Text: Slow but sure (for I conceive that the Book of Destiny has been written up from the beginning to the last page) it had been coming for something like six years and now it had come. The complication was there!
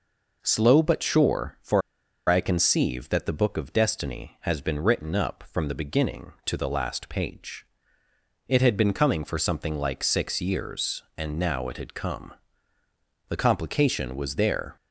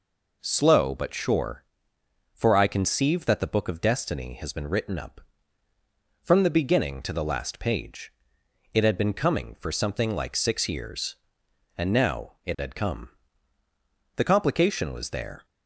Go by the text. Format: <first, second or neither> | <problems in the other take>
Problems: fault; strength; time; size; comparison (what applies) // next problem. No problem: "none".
second | pauses between "for" and "I"; noticeable; at 1.8 s; 0.48 s long